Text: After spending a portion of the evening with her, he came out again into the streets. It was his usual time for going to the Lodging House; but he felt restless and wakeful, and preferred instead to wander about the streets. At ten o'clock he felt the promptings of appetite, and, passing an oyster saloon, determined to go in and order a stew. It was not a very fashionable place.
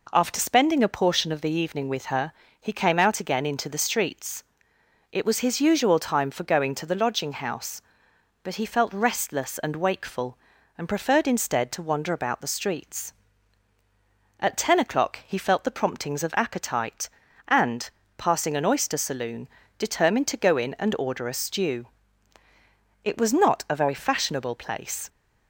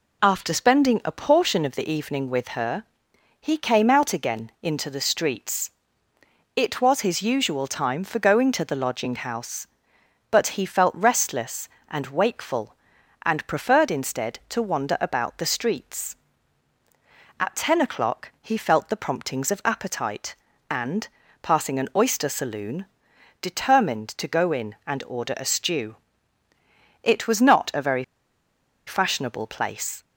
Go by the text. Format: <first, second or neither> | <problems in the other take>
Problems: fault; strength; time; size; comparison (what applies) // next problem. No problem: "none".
first | pauses between "very" and "fashionable"; noticeable; at 28.0 s; 0.82 s long